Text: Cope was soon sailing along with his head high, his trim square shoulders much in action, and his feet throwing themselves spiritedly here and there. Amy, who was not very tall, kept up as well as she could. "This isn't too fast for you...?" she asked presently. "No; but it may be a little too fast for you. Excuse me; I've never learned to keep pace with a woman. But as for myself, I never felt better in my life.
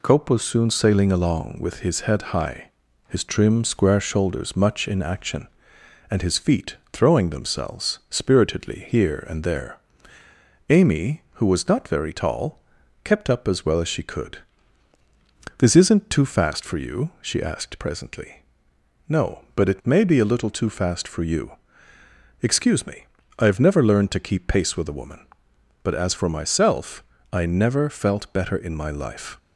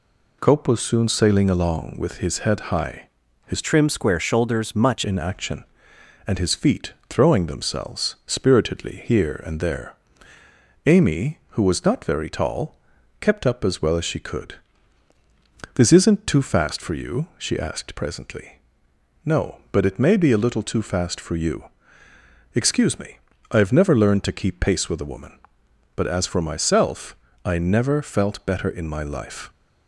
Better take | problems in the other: first | changes voice from "trim" to "much"; from 3.6 to 5.0 s; 1.4 s long // pauses between "feet" and "throwing"; slight; at 6.9 s; 0.16 s long; slight in the first

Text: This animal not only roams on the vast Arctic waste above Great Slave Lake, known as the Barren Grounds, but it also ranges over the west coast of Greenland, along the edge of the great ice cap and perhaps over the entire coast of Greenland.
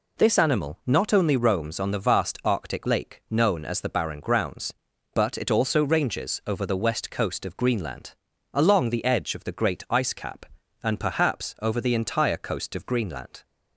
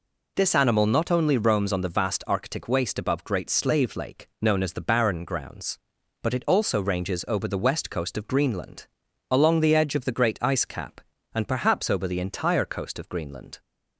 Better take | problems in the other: second | skips "waste above Great Slave"; at 2.8 s

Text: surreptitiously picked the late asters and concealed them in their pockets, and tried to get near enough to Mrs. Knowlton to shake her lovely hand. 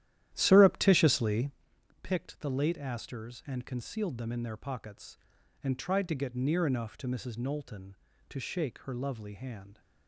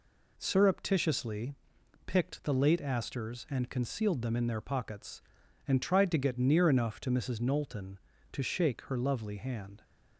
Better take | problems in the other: second | starts louder than the rest; strong; until 1.6 s; 12.5 dB // pauses between "surreptitiously" and "picked"; noticeable; at 1.5 s; 0.52 s long; noticeable in the second

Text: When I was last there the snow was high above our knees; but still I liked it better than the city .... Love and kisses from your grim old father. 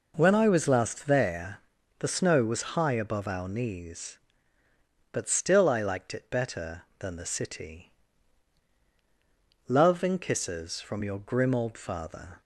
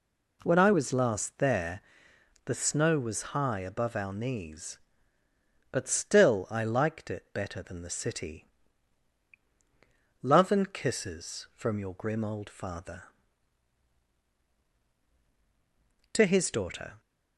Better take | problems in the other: first | pauses between "there" and "the"; noticeable; at 1.7 s; 0.64 s long; also in the first // goes on to say "TO HIS DAUGHTER"; noticeable; from 16.1 s on; 0.88 s long

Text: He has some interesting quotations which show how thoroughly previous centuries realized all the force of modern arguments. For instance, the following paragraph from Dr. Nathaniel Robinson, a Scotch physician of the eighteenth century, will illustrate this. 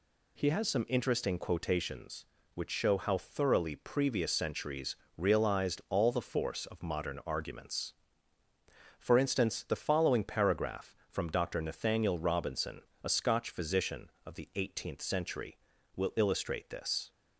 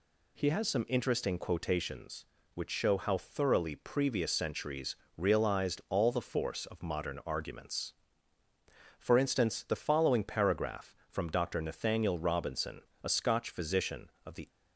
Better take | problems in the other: first | pauses between "centuries" and "realized"; slight; at 4.9 s; 0.22 s long; slight in the first // stops before "eighteenth century will illustrate this"; at 14.4 s

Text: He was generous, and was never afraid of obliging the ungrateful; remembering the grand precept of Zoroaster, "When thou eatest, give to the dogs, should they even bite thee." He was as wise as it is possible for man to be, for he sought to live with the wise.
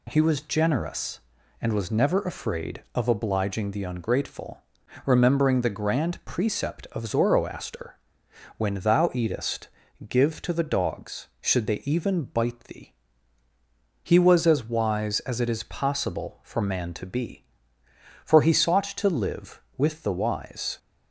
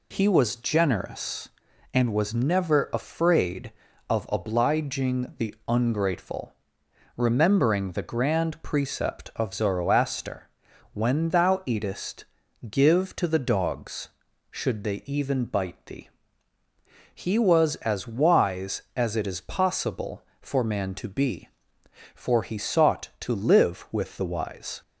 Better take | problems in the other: neither | none

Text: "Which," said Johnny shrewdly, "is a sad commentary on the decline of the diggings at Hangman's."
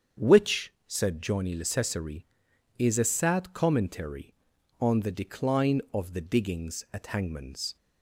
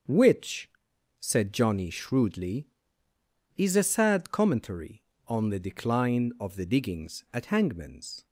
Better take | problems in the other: second | starts louder than the rest; strong; until 1.3 s; 7.5 dB; also in the second // says "lecessary" for "shrewdly"; at 1.5 s

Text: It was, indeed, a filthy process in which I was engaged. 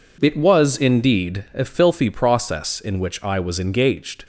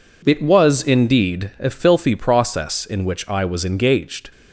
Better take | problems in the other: neither | none

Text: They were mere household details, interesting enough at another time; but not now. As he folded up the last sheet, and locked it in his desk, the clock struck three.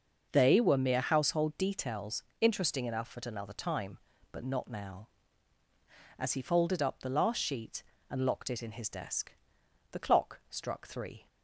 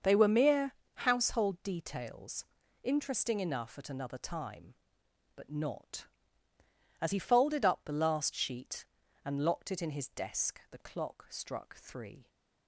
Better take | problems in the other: first | starts louder than the rest; until 1.2 s; 6.5 dB; noticeable in the first // pauses between "mere" and "household"; slight; at 0.7 s; 0.22 s long // skips "now"; at 6.5 s

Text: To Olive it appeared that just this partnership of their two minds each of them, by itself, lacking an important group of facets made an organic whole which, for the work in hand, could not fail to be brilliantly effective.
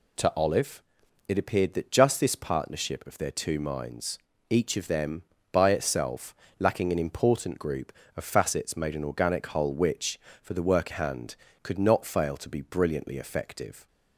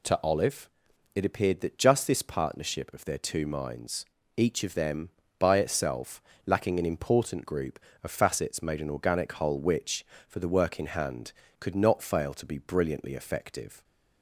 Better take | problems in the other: second | pauses between "Olive" and "it"; noticeable; at 0.8 s; 0.46 s long; noticeable in the second // pauses between "minds" and "each"; slight; at 4.1 s; 0.30 s long; slight in the second // skips "in"; at 10.9 s

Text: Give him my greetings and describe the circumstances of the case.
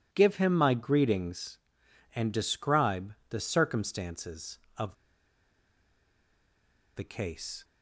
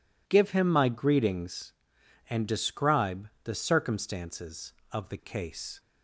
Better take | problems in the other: second | pauses between "describe" and "the"; slight; at 3.1 s; 0.16 s long; slight in the second // pauses between "of" and "the"; strong; at 4.9 s; 2.0 s long

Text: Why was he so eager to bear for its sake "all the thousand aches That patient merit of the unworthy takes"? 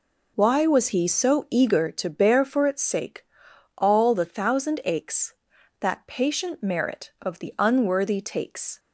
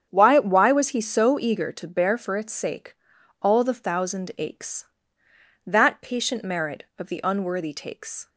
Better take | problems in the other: first | starts louder than the rest; strong; until 1.1 s; 8 dB // says "Why" twice; at 0.3 s // pauses between "sake" and "all"; noticeable; at 2.9 s; 0.46 s long; noticeable in the first

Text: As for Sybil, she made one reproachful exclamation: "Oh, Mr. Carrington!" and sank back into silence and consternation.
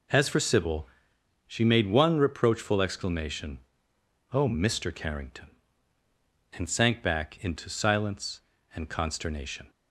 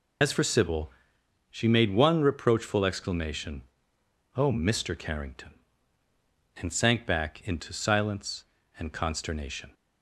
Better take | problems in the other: first | loses the start of "As"; at 0.2 s; 75 ms

